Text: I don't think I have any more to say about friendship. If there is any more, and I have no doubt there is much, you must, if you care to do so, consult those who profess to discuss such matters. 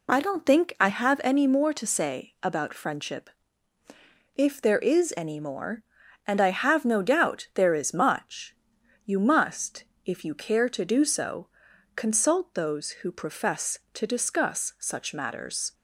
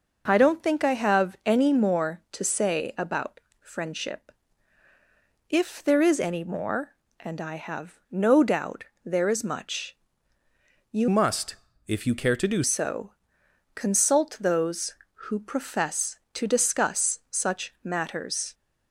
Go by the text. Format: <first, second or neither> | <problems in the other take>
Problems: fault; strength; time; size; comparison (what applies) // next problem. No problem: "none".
first | pauses between "about" and "friendship"; slight; at 3.3 s; 0.24 s long // pauses between "doubt" and "there"; slight; at 8.8 s; 0.20 s long // changes voice from "must" to "do"; from 11.0 to 12.6 s; 1.6 s long